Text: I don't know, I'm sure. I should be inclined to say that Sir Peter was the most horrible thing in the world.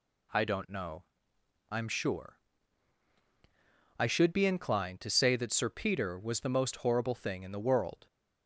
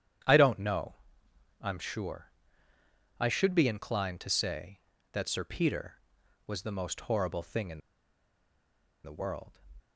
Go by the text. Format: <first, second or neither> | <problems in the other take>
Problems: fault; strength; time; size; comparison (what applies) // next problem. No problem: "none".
first | starts louder than the rest; strong; until 1.9 s; 9.5 dB // pauses between "in" and "the"; at 7.8 s; 1.2 s long